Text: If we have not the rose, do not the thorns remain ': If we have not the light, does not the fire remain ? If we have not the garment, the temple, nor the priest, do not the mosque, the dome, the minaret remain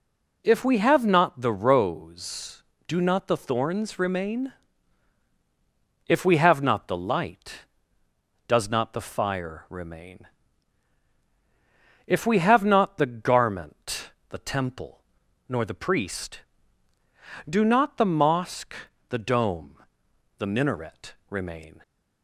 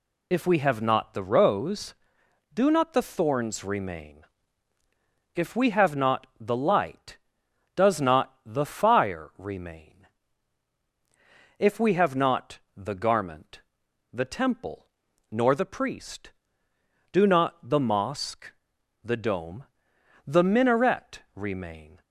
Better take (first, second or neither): first